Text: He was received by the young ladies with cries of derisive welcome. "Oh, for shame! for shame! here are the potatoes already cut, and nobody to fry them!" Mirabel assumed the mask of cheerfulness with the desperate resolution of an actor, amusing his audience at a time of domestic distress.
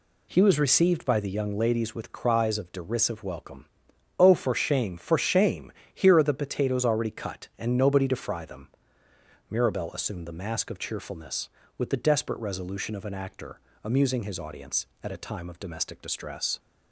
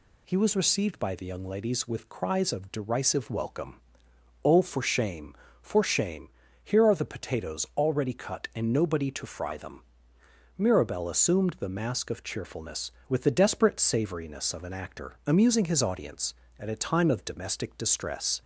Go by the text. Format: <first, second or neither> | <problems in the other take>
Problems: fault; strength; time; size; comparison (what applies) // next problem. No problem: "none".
first | says "savoriness" for "resolution"; at 13.7 s